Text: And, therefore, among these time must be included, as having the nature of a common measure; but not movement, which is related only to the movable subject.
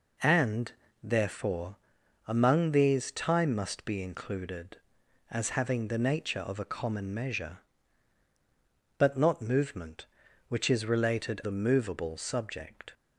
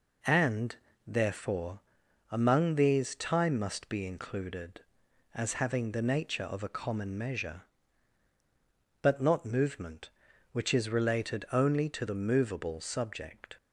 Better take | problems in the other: second | skips "only to"; at 11.4 s

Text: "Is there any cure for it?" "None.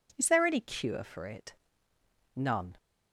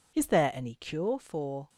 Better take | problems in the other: first | stops before "it None"; at 1.6 s

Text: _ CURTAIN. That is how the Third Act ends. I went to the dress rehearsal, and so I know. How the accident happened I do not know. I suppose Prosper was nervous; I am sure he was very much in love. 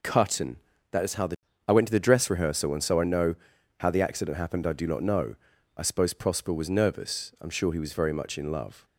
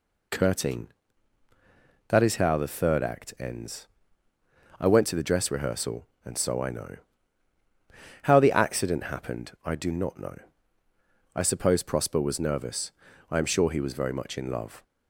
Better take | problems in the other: second | skips "Third Act ends"; at 1.5 s

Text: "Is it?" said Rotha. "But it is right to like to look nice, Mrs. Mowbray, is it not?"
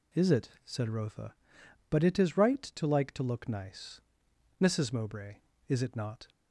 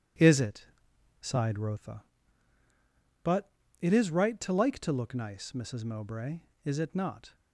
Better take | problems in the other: first | says "sighed" for "said"; at 1.2 s // pauses between "But" and "it"; slight; at 3.5 s; 0.30 s long

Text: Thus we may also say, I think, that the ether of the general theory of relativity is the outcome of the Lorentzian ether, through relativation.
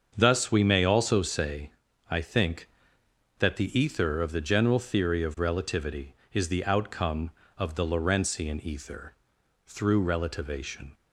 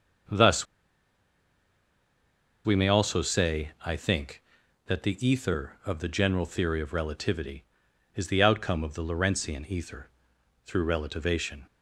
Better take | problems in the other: first | starts louder than the rest; until 3.2 s; 6.5 dB; also in the first // pauses between "Thus" and "we"; strong; at 0.6 s; 2.0 s long

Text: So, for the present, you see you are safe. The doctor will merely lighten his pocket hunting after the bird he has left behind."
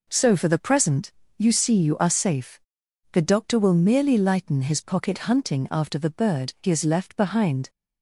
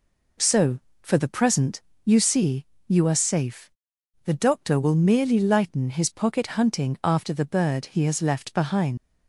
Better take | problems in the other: first | pauses between "see" and "you"; slight; at 2.6 s; 0.22 s long // leaves "behind" unfinished; at 8.9 s; 120 ms

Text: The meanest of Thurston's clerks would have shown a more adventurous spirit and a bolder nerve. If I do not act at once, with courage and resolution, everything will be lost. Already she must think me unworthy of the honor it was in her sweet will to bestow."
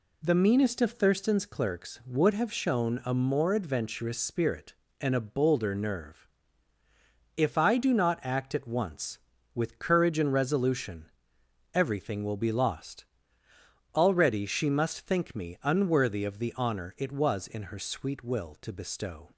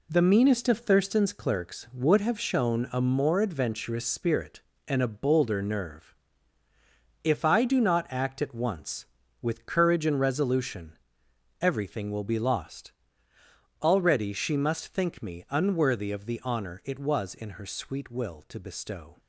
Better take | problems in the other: first | gets quieter; strong; throughout; 7.5 dB

